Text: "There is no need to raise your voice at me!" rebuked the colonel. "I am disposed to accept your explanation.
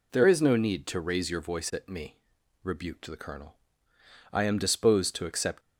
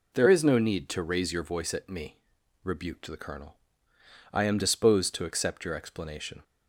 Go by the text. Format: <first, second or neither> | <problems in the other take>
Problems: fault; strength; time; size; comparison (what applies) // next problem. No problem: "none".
second | stops before "your explanation"; at 5.6 s